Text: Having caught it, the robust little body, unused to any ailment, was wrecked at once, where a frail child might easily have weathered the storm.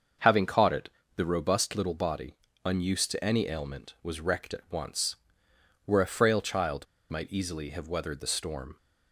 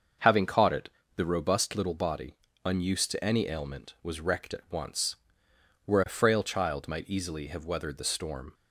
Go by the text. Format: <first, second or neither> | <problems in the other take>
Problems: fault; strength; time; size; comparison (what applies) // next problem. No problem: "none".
second | starts louder than the rest; until 1.4 s; 6.5 dB; also in the second // pauses between "child" and "might"; slight; at 6.8 s; 0.24 s long